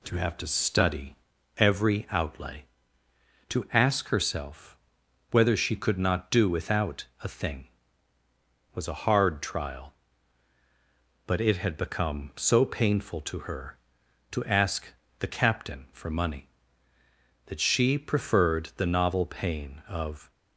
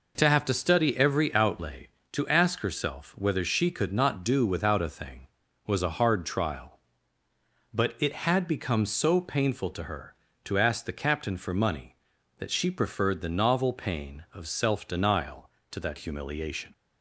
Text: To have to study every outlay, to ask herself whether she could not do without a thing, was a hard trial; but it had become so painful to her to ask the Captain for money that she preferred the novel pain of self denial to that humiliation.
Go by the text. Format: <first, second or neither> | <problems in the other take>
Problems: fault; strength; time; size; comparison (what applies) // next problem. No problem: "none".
second | pauses between "study" and "every"; at 1.1 s; 0.42 s long // pauses between "herself" and "whether"; noticeable; at 4.7 s; 0.54 s long // pauses between "ask" and "the"; slight; at 14.8 s; 0.32 s long // stops before "self denial to that humiliation"; at 20.3 s